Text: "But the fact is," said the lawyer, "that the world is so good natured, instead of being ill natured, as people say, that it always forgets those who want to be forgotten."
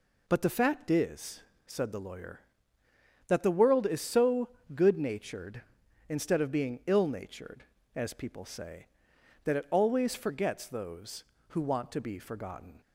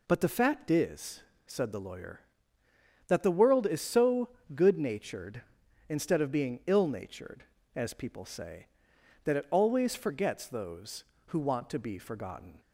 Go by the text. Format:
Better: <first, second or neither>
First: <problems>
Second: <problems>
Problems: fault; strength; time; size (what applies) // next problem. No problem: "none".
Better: neither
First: pauses between "so" and "good"; slight; at 4.4 s; 0.24 s long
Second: pauses between "so" and "good"; slight; at 4.2 s; 0.24 s long